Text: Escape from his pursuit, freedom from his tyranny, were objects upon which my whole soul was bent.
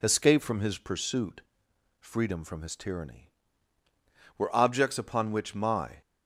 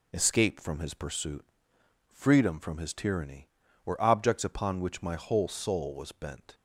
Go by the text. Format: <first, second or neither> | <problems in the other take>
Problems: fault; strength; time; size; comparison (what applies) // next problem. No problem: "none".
second | stops before "whole soul was bent"; at 6.0 s